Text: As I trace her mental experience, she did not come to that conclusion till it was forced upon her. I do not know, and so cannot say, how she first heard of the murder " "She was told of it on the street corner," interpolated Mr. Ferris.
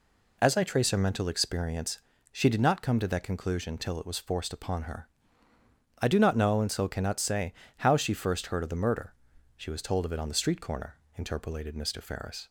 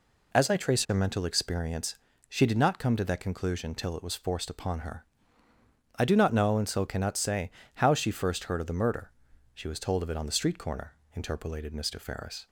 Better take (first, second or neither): neither